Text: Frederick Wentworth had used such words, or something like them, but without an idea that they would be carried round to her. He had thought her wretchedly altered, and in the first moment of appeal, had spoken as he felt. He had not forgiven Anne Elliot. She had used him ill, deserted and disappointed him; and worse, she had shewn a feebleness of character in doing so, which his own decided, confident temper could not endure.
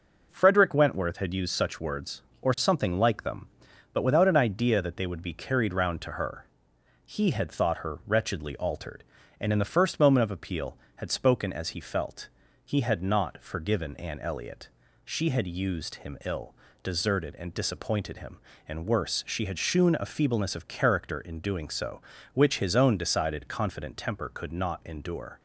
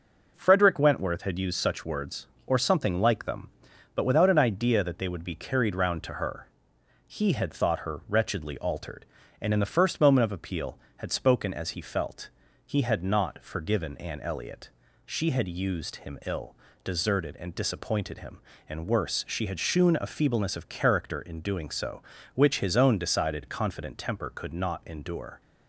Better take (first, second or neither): neither